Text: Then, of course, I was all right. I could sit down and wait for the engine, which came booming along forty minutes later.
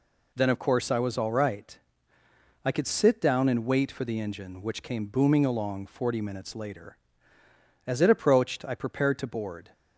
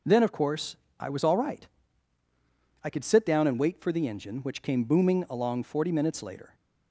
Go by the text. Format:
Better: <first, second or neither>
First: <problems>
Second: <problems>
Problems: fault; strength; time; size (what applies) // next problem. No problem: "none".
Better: second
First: goes on to say "As it approached I prepared to board"; strong; from 7.8 s on; 1.8 s long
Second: none